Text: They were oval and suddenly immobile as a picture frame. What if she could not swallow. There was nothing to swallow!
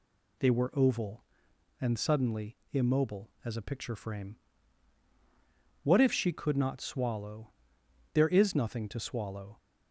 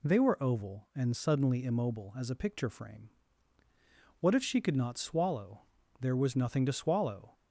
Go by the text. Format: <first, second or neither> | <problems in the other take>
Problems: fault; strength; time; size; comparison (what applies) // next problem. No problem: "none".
second | pauses between "suddenly" and "immobile"; slight; at 2.5 s; 0.16 s long // says "is" for "was"; at 8.2 s